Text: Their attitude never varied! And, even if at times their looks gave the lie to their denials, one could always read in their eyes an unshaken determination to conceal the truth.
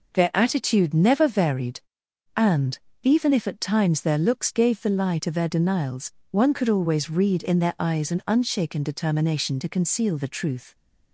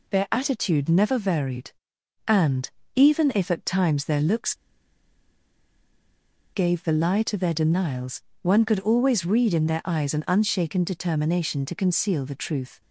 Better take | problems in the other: first | pauses between "looks" and "gave"; strong; at 4.5 s; 2.0 s long

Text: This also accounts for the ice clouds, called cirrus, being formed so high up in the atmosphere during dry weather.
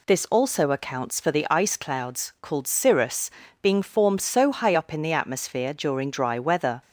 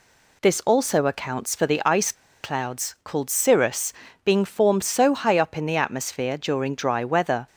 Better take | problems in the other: first | pauses between "ice" and "clouds"; slight; at 2.1 s; 0.30 s long

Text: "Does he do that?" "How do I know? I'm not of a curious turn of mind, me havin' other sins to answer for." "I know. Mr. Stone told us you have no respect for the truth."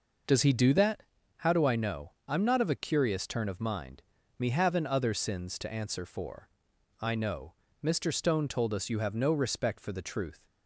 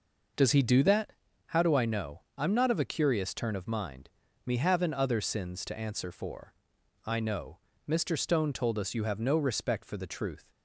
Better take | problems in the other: neither | none

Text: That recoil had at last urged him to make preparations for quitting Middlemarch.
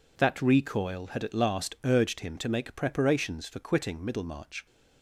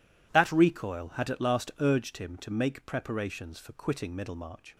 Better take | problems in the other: neither | none

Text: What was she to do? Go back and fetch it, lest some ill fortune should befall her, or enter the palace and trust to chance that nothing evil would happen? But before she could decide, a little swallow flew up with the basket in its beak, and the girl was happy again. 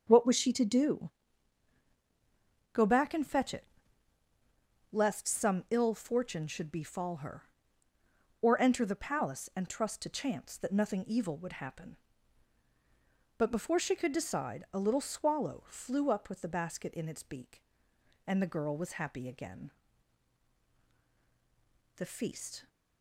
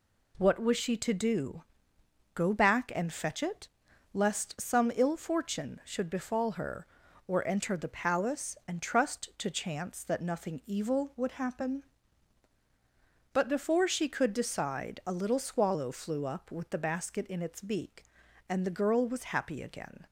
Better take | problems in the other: second | starts louder than the rest; until 1.0 s; 7 dB // goes on to say "The feast"; noticeable; from 21.9 s on; 0.72 s long

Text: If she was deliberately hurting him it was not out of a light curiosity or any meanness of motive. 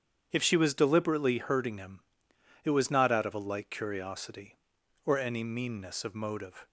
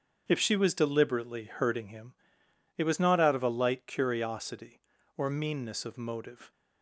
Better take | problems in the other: first | starts louder than the rest; strong; until 1.2 s; 7.5 dB; strong in the first // pauses between "him" and "it"; noticeable; at 2.1 s; 0.62 s long; noticeable in the first // skips "any"; at 5.2 s

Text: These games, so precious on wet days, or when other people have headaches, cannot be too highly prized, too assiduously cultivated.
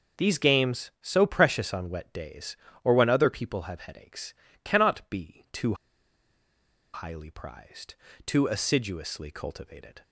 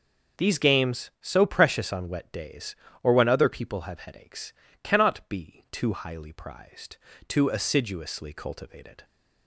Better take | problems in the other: second | pauses between "too" and "highly"; at 5.7 s; 1.2 s long

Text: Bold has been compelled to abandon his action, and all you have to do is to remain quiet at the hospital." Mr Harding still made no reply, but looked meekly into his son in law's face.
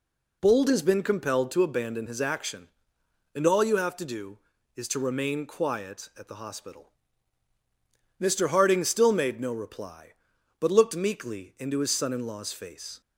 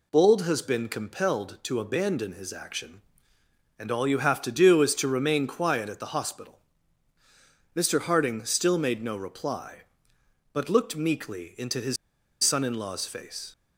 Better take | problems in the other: first | pauses between "his" and "son"; noticeable; at 11.9 s; 0.47 s long

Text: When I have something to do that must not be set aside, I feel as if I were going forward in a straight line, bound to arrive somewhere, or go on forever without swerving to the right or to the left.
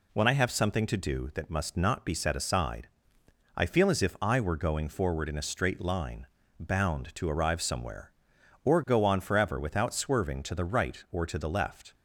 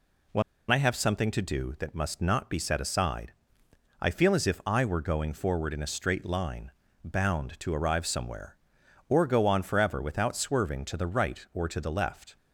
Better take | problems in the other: first | pauses between "When" and "I"; slight; at 0.4 s; 0.27 s long

